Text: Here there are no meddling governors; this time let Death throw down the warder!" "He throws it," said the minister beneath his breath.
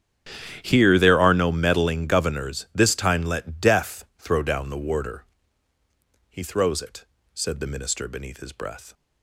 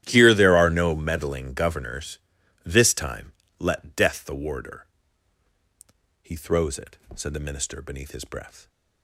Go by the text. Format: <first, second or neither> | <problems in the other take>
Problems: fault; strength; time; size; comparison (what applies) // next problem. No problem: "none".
first | starts louder than the rest; strong; until 1.0 s; 12 dB; strong in the first // pauses between "time" and "let"; slight; at 3.3 s; 0.26 s long // skips "throw down"; at 4.2 s